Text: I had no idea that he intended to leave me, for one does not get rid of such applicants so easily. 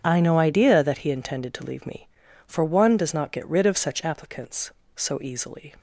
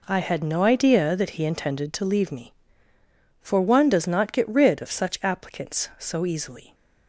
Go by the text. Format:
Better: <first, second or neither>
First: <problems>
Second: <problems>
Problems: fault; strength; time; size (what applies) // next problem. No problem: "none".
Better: second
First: starts louder than the rest; strong; until 1.0 s; 8 dB // skips "had"; at 0.1 s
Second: none